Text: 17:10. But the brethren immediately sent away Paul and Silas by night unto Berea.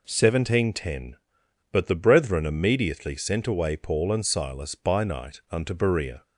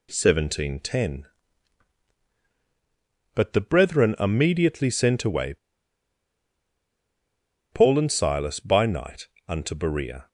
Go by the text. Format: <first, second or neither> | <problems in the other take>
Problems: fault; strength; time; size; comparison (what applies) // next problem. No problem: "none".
first | pauses between "away" and "Paul"; strong; at 5.5 s; 2.2 s long // pauses between "night" and "unto"; slight; at 9.2 s; 0.22 s long